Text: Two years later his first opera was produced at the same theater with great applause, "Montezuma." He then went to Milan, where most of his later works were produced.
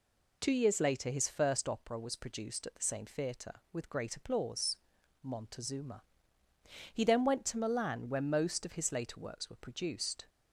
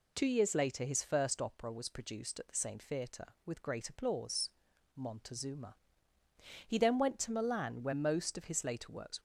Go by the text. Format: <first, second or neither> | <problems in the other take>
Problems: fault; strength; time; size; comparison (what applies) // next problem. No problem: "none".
first | stops before "were produced"; at 9.1 s